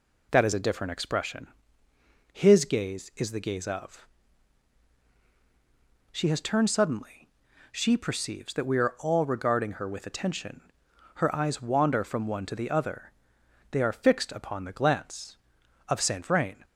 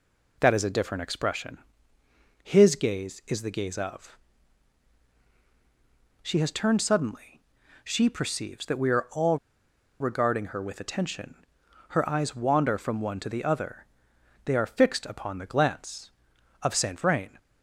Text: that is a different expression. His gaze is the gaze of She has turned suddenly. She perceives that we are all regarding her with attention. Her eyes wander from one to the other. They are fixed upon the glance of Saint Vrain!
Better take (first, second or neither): first